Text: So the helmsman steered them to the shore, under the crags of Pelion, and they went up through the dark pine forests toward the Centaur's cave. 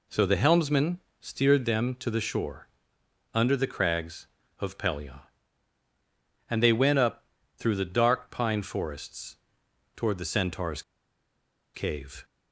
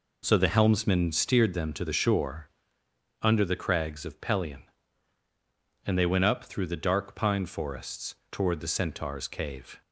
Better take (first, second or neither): second